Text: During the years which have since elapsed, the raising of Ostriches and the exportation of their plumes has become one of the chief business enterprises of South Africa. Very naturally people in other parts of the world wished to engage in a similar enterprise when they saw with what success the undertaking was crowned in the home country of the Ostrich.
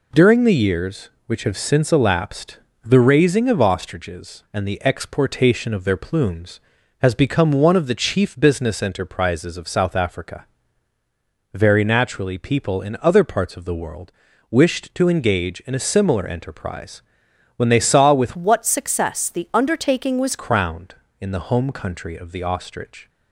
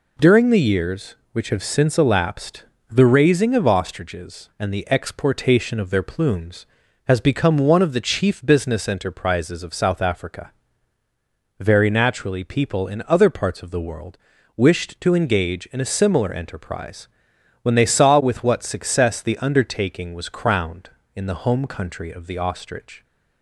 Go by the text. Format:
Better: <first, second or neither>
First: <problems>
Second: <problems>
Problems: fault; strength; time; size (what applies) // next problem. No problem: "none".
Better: second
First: pauses between "world" and "wished"; at 14.1 s; 0.40 s long // pauses between "enterprise" and "when"; noticeable; at 17.0 s; 0.52 s long // changes voice from "what" to "was"; from 18.3 to 20.3 s; 2.0 s long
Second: pauses between "world" and "wished"; at 14.1 s; 0.40 s long // pauses between "enterprise" and "when"; noticeable; at 17.0 s; 0.52 s long